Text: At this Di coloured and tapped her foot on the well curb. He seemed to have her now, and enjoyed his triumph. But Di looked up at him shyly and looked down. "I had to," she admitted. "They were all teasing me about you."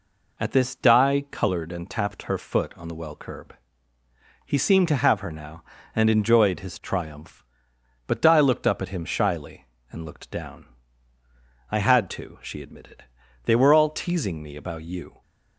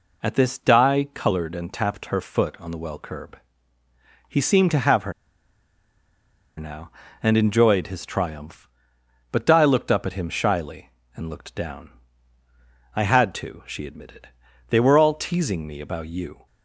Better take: first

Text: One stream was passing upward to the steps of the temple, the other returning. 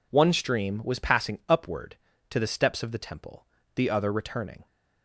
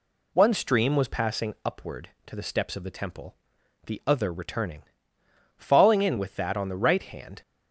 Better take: first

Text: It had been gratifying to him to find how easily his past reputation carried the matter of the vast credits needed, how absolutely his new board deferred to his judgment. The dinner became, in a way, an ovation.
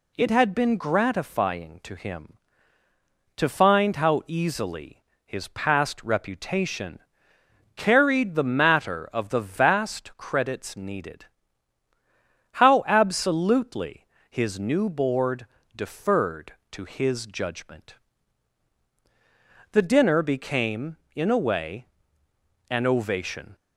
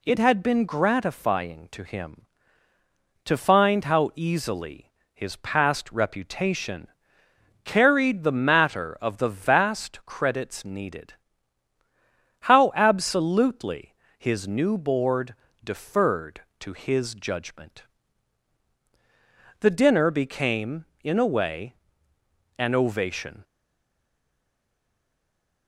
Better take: first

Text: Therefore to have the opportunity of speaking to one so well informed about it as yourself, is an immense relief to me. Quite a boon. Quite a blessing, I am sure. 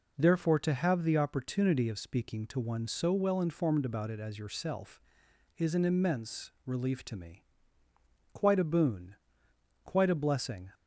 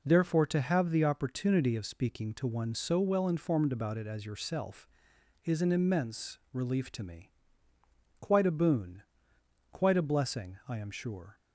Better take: second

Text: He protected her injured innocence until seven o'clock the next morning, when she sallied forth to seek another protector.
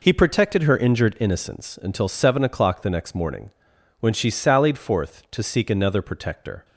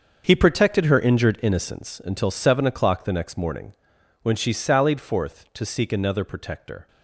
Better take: first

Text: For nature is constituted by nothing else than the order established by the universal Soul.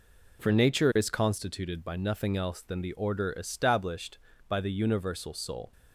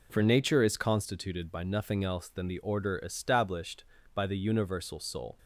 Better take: neither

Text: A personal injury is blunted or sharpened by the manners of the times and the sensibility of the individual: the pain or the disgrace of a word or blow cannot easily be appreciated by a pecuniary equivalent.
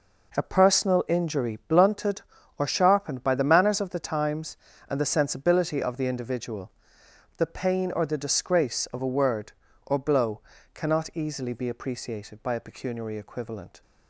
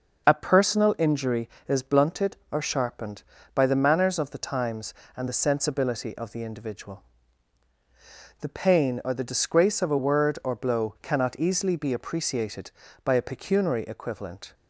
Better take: second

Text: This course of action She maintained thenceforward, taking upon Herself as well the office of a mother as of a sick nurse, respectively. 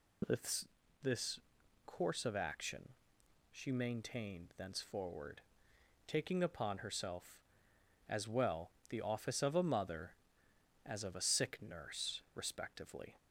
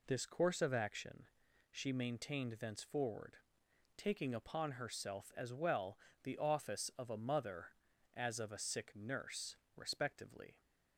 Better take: second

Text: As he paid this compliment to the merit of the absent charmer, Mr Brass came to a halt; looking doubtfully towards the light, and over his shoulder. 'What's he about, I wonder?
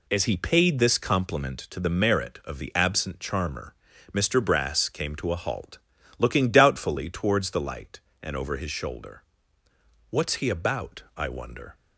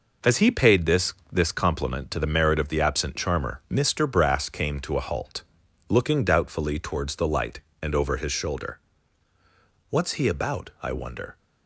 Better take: first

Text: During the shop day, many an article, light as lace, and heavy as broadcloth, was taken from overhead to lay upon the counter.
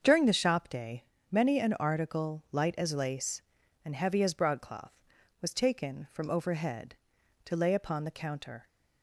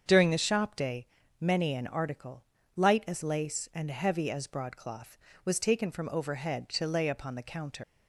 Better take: first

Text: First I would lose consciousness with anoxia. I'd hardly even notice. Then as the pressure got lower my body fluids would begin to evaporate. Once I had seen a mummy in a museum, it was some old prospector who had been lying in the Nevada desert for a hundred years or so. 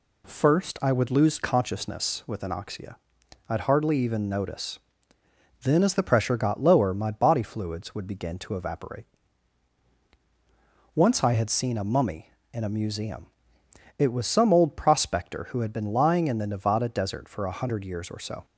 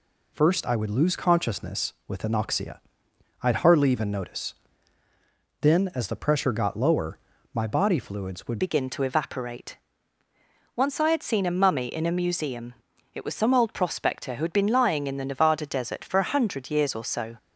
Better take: first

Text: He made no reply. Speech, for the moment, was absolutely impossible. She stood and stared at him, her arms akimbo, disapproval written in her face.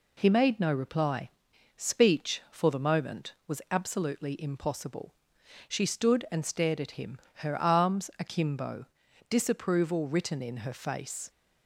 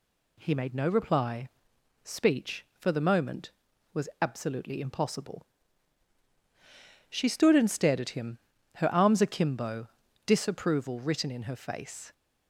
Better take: neither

